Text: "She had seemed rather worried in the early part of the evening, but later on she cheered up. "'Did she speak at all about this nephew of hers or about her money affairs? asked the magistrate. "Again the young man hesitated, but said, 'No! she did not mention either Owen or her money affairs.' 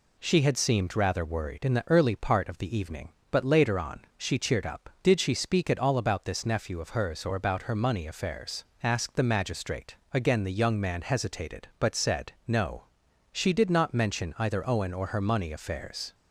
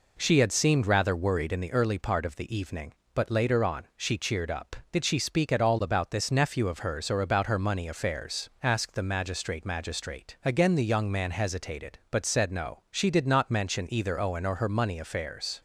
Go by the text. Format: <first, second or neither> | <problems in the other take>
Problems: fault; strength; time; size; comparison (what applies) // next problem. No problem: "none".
first | says "magistrate" twice; at 9.6 s